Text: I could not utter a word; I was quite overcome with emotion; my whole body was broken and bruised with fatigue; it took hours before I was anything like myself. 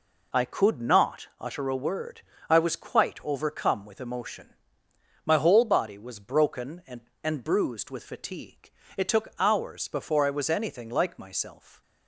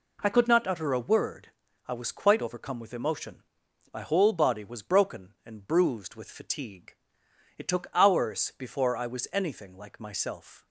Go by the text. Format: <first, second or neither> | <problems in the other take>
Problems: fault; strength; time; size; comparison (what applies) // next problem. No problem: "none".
second | says "and" twice; at 7.2 s